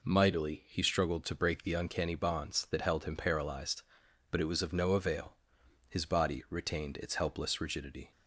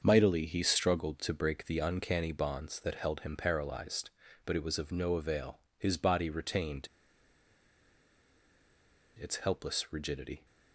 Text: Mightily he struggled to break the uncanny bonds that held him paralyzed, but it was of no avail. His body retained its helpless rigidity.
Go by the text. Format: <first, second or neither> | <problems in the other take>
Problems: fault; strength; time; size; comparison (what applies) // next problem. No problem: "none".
first | starts louder than the rest; until 1.0 s; 6.5 dB // pauses between "retained" and "its"; strong; at 6.8 s; 2.3 s long